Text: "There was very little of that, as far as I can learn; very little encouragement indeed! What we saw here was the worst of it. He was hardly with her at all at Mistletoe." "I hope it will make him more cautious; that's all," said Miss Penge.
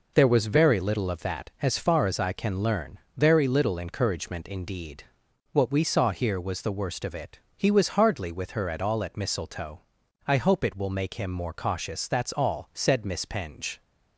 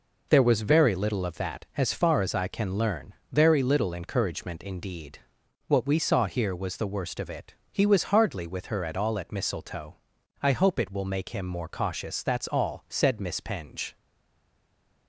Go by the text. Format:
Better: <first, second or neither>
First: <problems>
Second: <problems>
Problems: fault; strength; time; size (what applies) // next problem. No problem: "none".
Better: first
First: none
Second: stays silent after the last word; from 13.9 s on; 1.1 s long